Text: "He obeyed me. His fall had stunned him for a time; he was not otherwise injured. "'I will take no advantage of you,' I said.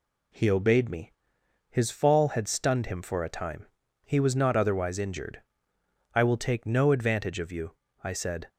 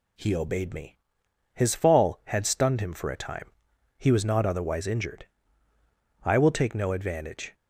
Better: first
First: none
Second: stops before "of you I said"; at 7.5 s

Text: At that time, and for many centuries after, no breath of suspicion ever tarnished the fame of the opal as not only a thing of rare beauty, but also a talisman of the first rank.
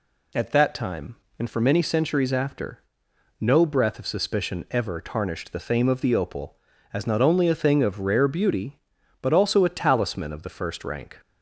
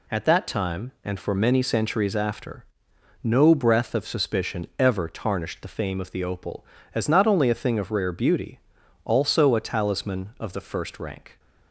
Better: first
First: none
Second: skips "but"; at 8.8 s

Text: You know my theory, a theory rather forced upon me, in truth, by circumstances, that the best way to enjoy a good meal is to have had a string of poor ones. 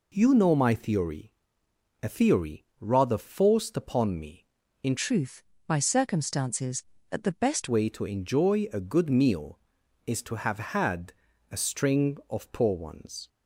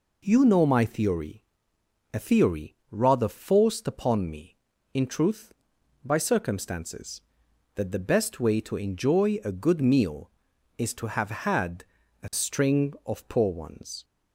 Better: second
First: changes voice from "truth" to "best"; from 4.9 to 7.6 s; 2.7 s long // pauses between "had" and "a"; at 11.1 s; 0.38 s long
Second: pauses between "had" and "a"; at 11.8 s; 0.38 s long

